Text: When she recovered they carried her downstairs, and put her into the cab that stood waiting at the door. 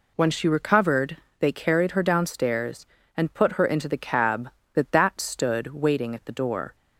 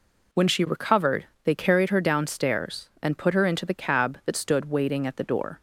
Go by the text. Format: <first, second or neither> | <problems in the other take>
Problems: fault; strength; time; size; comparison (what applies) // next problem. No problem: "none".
second | pauses between "recovered" and "they"; slight; at 1.1 s; 0.22 s long; slight in the second // says "that" twice; at 4.9 s